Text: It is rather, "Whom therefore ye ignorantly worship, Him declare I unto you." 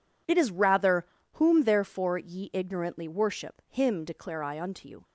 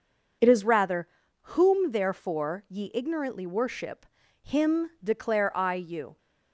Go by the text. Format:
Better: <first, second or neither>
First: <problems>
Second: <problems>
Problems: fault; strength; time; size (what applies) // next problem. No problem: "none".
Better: first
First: none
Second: skips "unto"; at 5.7 s